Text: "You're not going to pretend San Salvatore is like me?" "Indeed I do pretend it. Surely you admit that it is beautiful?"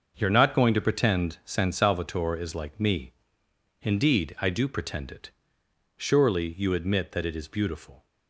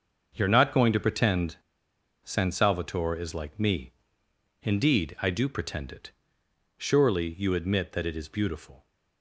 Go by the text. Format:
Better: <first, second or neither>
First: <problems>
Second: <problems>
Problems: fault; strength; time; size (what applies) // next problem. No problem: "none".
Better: first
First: starts louder than the rest; until 1.2 s; 6.5 dB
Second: starts louder than the rest; until 1.3 s; 6.5 dB // pauses between "pretend" and "San"; noticeable; at 1.5 s; 0.66 s long